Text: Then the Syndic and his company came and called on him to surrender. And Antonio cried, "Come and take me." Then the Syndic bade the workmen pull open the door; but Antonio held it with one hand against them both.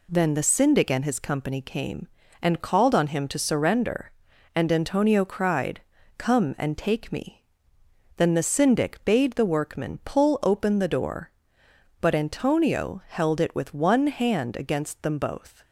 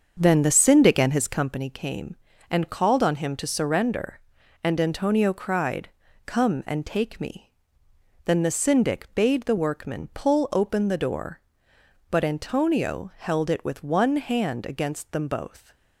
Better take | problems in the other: first | starts louder than the rest; until 1.6 s; 7 dB

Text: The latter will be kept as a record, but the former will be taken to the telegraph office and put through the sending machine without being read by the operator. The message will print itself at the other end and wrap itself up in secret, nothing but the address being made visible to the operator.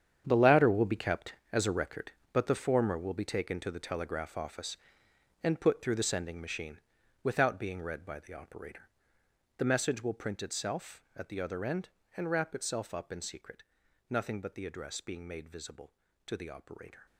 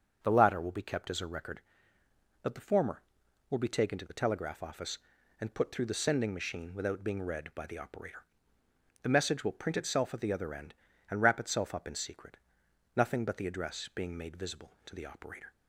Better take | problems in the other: second | gets quieter; strong; throughout; 13.5 dB // starts louder than the rest; strong; until 1.2 s; 8.5 dB; also in the second // pauses between "machine" and "without"; at 6.7 s; 0.44 s long

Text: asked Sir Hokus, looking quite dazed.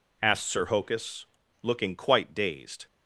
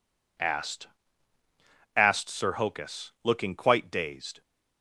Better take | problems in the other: first | says "asked" twice; at 1.9 s

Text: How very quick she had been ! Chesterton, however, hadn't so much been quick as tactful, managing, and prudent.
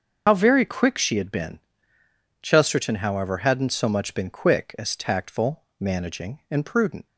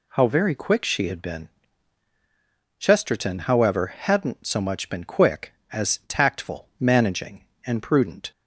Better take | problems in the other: second | loses the start of "How"; at 0.2 s; 65 ms // starts louder than the rest; until 1.2 s; 6.5 dB

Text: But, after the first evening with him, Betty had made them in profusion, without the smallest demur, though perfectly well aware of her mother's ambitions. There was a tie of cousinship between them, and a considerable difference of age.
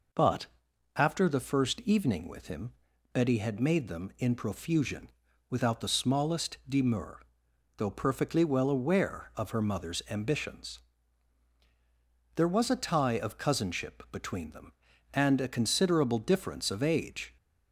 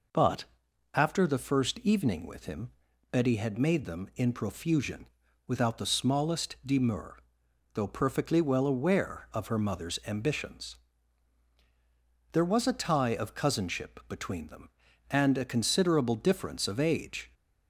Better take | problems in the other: neither | none

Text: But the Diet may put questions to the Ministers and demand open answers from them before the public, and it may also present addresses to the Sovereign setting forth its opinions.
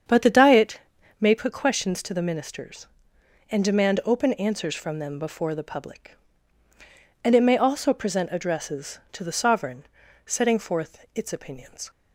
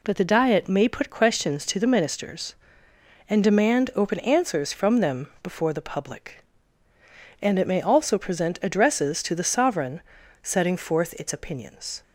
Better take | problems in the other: second | starts louder than the rest; strong; until 1.4 s; 7.5 dB // pauses between "Diet" and "may"; at 0.8 s; 0.38 s long // pauses between "Sovereign" and "setting"; at 9.8 s; 0.42 s long; also in the second

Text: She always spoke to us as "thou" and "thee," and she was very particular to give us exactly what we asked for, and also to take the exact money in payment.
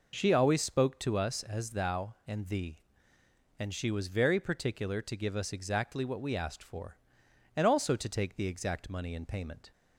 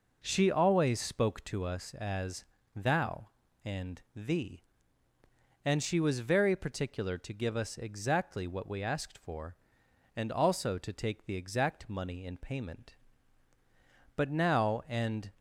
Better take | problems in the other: first | pauses between "as" and "thou"; slight; at 2.4 s; 0.32 s long // goes on to say "But now and"; noticeable; from 14.1 s on; 1.1 s long

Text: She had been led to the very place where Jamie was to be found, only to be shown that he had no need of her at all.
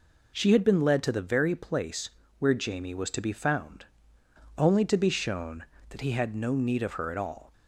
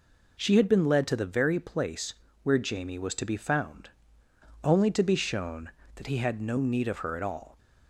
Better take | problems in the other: neither | pauses between "place" and "where"; slight; the same in both

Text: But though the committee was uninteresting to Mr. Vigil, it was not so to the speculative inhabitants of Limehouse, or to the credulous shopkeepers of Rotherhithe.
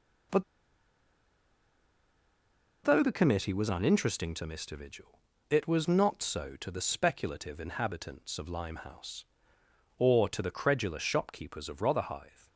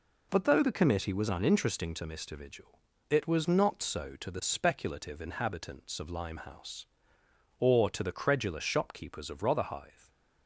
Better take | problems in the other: second | pauses between "But" and "though"; strong; at 0.4 s; 2.4 s long

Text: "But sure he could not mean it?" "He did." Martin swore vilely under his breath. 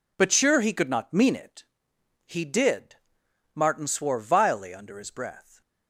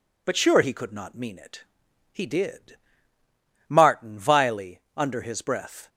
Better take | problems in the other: first | skips "swore"; at 4.1 s // pauses between "vilely" and "under"; slight; at 4.7 s; 0.18 s long

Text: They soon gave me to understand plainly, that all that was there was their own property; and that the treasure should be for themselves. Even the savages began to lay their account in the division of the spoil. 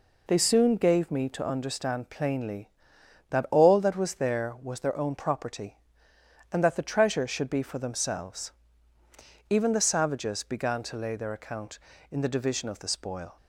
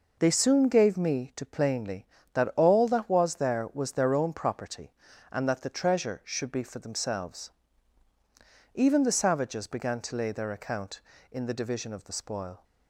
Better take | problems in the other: first | skips "understand"; at 1.4 s

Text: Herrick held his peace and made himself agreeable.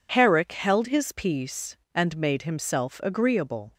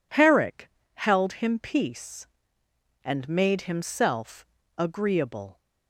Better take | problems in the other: first | pauses between "Herrick" and "held"; slight; at 0.6 s; 0.25 s long // says "him" for "his"; at 1.3 s // pauses between "himself" and "agreeable"; slight; at 4.4 s; 0.32 s long

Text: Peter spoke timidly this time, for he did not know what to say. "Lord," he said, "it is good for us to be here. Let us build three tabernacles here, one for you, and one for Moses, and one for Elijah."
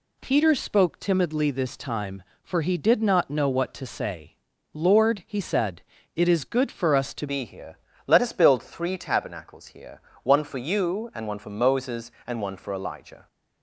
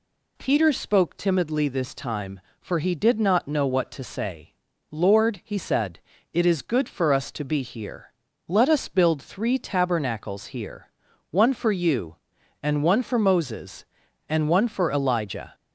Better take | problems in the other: second | changes voice at "be"; from 7.2 s on; 6.0 s long

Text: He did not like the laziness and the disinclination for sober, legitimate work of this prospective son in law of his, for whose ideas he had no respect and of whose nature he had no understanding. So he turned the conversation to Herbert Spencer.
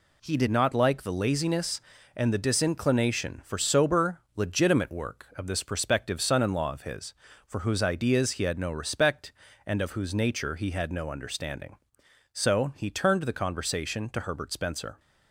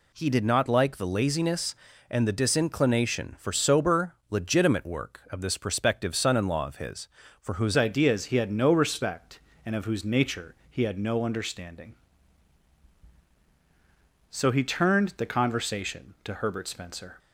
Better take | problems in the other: first | changes voice at "ideas"; from 7.7 s on; 9.4 s long // pauses between "nature" and "he"; slight; at 10.5 s; 0.16 s long

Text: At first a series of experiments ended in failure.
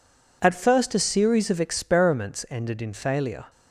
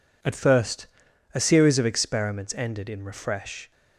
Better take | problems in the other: first | pauses between "first" and "a"; noticeable; at 0.8 s; 0.48 s long // says "refresh" for "failure"; at 3.0 s

